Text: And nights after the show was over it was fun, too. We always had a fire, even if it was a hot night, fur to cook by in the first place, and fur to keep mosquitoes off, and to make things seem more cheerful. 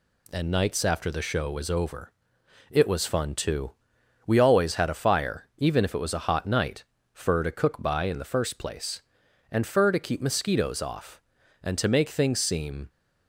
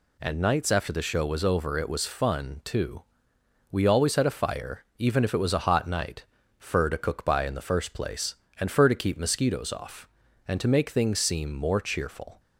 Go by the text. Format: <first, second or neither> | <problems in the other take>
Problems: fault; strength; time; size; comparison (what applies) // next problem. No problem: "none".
second | pauses between "over" and "it"; noticeable; at 2.1 s; 0.58 s long // stops before "more cheerful"; at 12.8 s